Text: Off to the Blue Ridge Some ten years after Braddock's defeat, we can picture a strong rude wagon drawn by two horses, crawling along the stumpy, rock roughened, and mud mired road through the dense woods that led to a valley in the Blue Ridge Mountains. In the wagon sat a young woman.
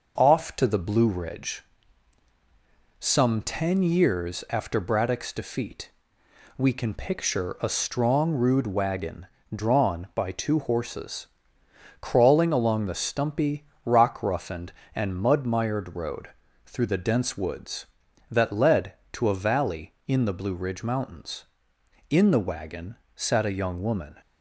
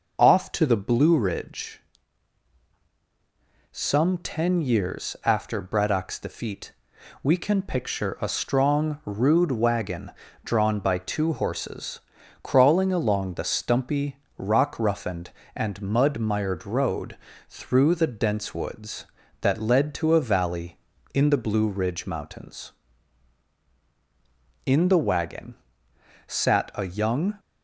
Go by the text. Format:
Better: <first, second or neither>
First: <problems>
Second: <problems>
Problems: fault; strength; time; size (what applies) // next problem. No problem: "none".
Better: first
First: pauses between "Ridge" and "Some"; strong; at 1.6 s; 1.3 s long // pauses between "wagon" and "drawn"; slight; at 9.2 s; 0.28 s long // pauses between "road" and "through"; slight; at 16.3 s; 0.34 s long // pauses between "wagon" and "sat"; slight; at 22.9 s; 0.20 s long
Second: pauses between "Ridge" and "Some"; strong; at 1.8 s; 1.9 s long // pauses between "wagon" and "drawn"; slight; at 10.1 s; 0.34 s long // pauses between "road" and "through"; slight; at 17.1 s; 0.32 s long // pauses between "wagon" and "sat"; noticeable; at 25.5 s; 0.72 s long // stops before "woman"; at 27.3 s